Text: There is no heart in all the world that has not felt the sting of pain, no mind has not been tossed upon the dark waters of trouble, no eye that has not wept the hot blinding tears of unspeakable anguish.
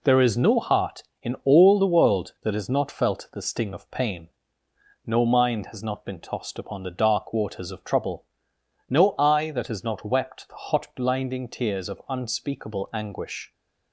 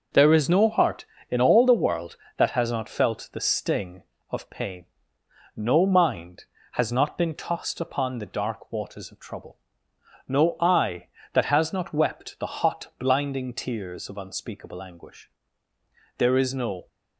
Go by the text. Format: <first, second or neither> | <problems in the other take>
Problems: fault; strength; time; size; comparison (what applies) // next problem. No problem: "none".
first | goes on to say "There is no"; noticeable; from 16.1 s on; 0.70 s long